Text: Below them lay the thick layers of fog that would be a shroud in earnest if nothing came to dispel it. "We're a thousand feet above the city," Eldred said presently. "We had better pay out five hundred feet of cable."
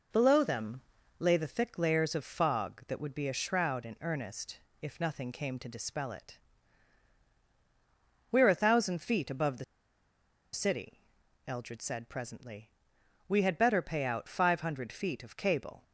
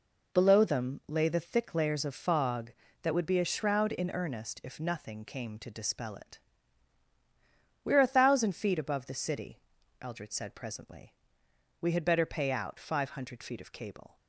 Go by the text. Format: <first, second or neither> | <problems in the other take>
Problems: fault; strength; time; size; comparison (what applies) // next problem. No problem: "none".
second | pauses between "them" and "lay"; at 0.8 s; 0.38 s long // pauses between "earnest" and "if"; slight; at 4.5 s; 0.22 s long // pauses between "the" and "city"; noticeable; at 9.6 s; 0.89 s long